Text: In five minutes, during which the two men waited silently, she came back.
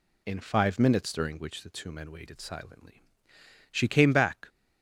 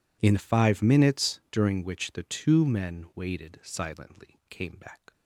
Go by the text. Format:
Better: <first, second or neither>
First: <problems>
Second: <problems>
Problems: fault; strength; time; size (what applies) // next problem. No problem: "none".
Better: first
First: none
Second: skips "she"; at 4.4 s